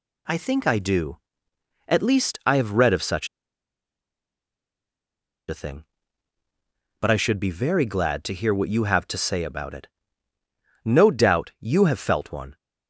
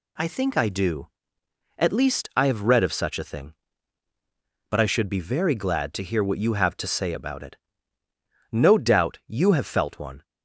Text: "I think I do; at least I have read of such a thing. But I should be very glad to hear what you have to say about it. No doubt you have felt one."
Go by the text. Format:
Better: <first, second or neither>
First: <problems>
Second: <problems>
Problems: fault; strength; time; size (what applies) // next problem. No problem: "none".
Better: second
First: pauses between "such" and "a"; strong; at 3.2 s; 2.2 s long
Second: none